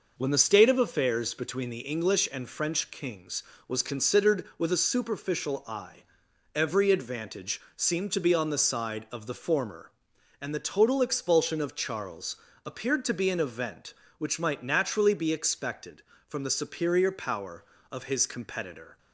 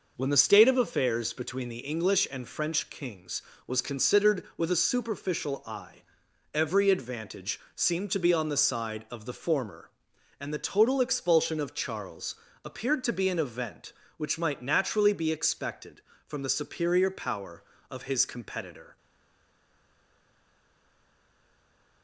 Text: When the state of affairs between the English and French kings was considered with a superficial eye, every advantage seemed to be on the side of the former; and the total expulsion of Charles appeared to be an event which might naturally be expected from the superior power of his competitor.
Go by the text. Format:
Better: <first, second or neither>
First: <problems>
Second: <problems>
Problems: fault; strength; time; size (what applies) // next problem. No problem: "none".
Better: first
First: pauses between "Charles" and "appeared"; slight; at 12.3 s; 0.30 s long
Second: pauses between "Charles" and "appeared"; slight; at 12.3 s; 0.30 s long // stays silent after the last word; strong; from 18.9 s on; 3.1 s long